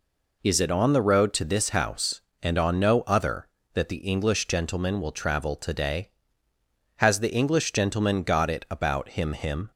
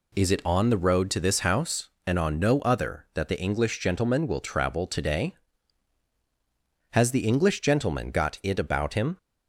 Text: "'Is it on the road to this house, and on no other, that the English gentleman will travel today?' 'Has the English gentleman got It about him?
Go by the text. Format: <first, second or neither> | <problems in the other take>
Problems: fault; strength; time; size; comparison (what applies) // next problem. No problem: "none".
second | says "him" twice; at 9.3 s